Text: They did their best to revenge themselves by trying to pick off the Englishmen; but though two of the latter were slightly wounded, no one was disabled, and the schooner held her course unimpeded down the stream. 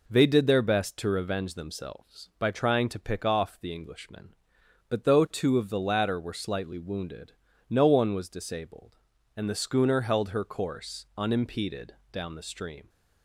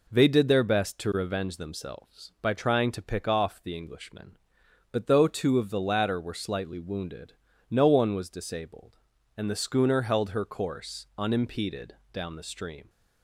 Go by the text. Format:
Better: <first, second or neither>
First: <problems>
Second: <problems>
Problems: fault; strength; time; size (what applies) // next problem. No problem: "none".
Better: neither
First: pauses between "unimpeded" and "down"; slight; at 11.9 s; 0.18 s long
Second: pauses between "unimpeded" and "down"; slight; at 11.9 s; 0.18 s long